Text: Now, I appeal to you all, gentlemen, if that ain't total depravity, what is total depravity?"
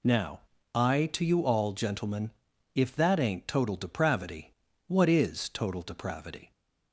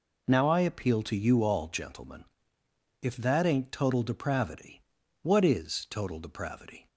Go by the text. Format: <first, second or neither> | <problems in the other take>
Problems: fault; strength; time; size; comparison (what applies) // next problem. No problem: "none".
second | skips "appeal"; at 1.1 s